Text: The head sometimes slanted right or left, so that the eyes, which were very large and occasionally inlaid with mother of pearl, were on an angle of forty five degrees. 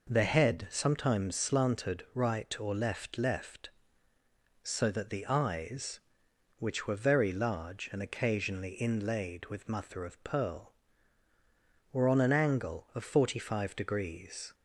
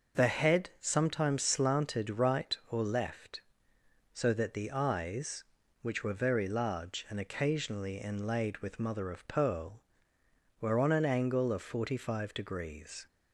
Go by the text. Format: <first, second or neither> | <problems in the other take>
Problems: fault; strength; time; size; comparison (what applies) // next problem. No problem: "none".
second | says "left" twice; at 3.1 s